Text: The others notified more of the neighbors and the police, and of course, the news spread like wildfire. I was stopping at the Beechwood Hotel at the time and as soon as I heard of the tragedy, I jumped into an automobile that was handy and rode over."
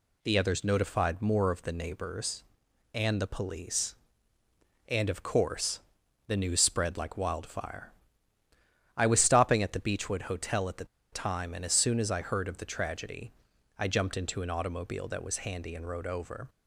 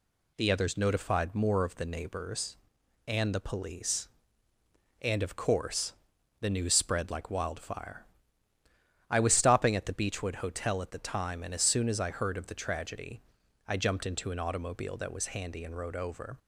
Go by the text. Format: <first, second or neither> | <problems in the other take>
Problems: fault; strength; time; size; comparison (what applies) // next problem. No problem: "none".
second | pauses between "the" and "time"; slight; at 10.8 s; 0.27 s long